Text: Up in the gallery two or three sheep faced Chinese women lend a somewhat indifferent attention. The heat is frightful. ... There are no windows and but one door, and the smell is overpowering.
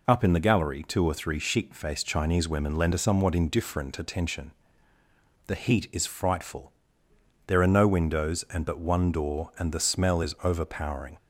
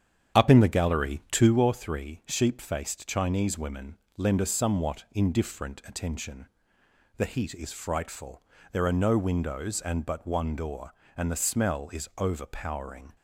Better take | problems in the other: first | starts louder than the rest; strong; until 1.6 s; 9 dB // pauses between "women" and "lend"; slight; at 3.9 s; 0.22 s long

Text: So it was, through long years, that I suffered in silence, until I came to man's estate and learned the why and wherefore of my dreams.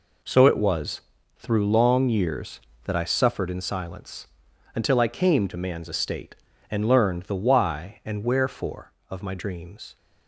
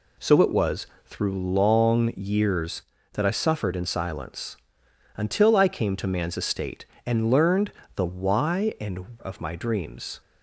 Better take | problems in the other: first | pauses between "learned" and "the"; slight; at 7.7 s; 0.24 s long // skips "wherefore"; at 9.1 s

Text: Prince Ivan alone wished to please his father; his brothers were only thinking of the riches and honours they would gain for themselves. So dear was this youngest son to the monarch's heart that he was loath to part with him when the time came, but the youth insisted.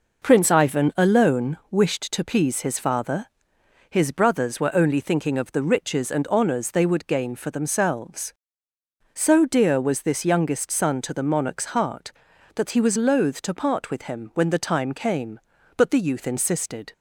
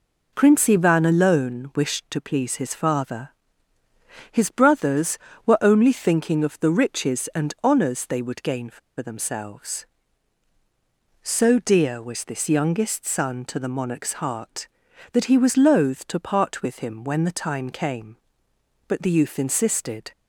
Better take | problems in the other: first | pauses between "for" and "themselves"; slight; at 8.7 s; 0.20 s long

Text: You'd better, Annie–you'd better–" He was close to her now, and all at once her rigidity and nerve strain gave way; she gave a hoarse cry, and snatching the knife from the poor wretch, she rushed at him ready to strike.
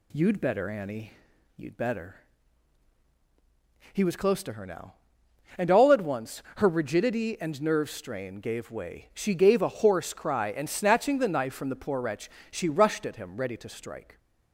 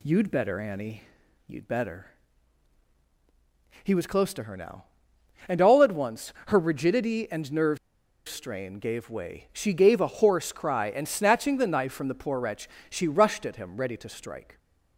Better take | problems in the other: first | pauses between "nerve" and "strain"; noticeable; at 7.7 s; 0.50 s long

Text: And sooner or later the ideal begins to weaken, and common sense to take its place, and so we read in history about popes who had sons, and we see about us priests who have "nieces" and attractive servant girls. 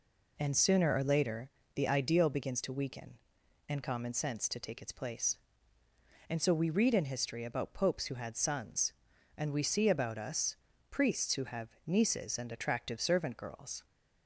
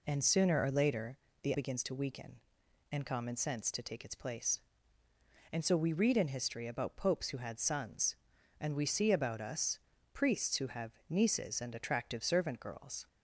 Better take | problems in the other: first | pauses between "later" and "the"; slight; at 1.1 s; 0.26 s long; slight in the first // skips "ideal"; at 1.5 s // pauses between "us" and "priests"; slight; at 9.7 s; 0.34 s long; slight in the first // pauses between "have" and "nieces"; slight; at 10.9 s; 0.16 s long; slight in the first

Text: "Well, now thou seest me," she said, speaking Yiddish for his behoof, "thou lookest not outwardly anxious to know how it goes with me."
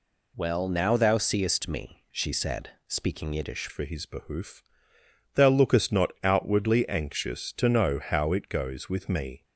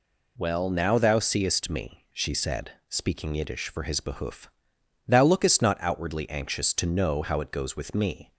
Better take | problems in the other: second | changes voice at "for"; from 3.6 s on; 5.8 s long

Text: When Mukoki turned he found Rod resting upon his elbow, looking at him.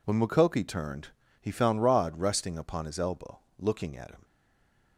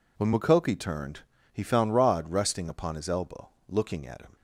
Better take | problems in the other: second | pauses between "turned" and "he"; slight; at 1.0 s; 0.32 s long; slight in the second // stays silent after the last word; slight; from 4.2 s on; 0.7 s long

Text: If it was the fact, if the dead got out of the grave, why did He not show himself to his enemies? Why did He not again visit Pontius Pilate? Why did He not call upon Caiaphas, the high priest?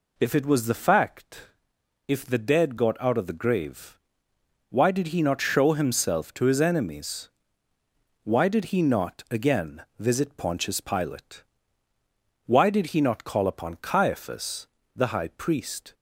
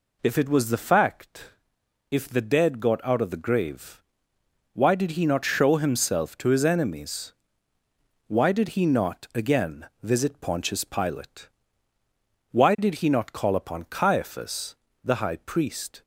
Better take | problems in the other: neither | pauses between "again" and "visit"; slight; the same in both

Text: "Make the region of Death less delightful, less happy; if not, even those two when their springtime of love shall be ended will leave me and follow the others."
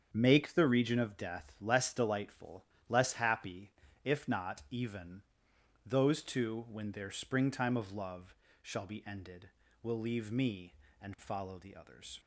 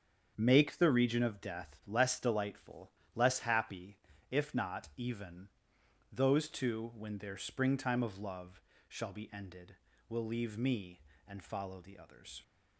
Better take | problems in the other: neither | starts louder than the rest; strong; the same in both // pauses between "even" and "those"; noticeable; the same in both // pauses between "love" and "shall"; slight; the same in both

